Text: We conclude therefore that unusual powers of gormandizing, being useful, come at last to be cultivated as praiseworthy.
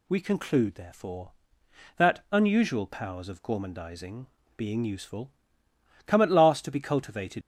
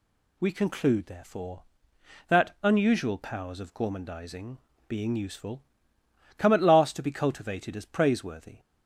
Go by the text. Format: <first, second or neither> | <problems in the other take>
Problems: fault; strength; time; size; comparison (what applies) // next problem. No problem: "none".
second | stops before "as praiseworthy"; at 7.4 s